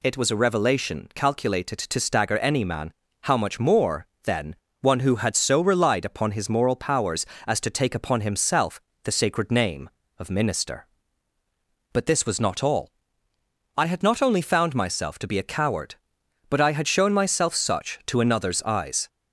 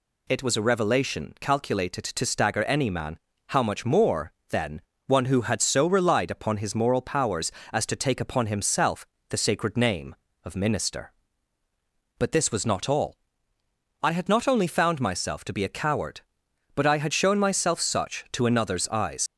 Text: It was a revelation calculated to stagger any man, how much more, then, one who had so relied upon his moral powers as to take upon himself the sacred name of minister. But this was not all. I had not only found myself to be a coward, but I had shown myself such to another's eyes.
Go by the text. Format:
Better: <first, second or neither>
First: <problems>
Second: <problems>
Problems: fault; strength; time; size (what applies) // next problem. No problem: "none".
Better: first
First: pauses between "himself" and "the"; slight; at 8.7 s; 0.24 s long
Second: pauses between "himself" and "the"; slight; at 9.0 s; 0.24 s long // leaves "eyes" unfinished; at 19.2 s; 70 ms